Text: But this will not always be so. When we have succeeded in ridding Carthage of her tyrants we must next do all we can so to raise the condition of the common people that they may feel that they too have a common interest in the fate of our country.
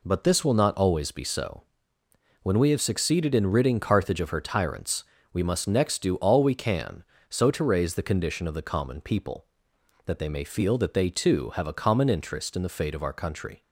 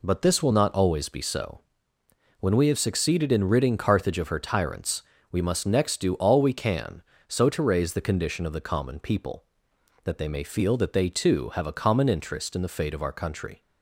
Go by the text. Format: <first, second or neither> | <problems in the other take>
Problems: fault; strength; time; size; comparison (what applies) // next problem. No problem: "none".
neither | pauses between "tyrants" and "we"; slight; the same in both